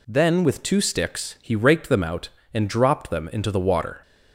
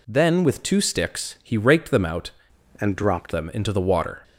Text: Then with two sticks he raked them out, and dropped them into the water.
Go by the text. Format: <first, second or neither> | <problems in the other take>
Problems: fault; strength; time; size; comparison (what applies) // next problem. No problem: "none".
first | changes voice from "and" to "dropped"; from 2.7 to 3.3 s; 0.6 s long